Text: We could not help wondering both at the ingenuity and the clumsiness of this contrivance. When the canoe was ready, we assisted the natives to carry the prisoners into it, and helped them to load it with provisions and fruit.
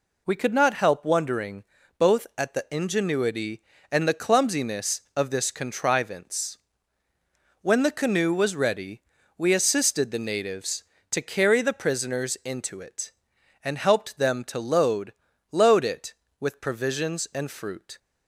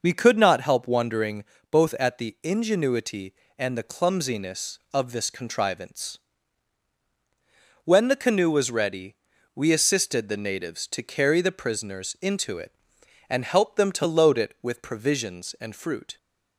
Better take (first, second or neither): second